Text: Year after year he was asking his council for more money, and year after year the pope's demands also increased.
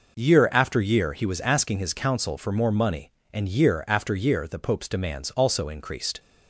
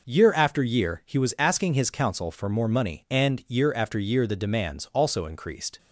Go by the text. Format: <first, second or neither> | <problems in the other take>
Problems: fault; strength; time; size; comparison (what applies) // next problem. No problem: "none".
first | skips "pope's"; at 4.3 s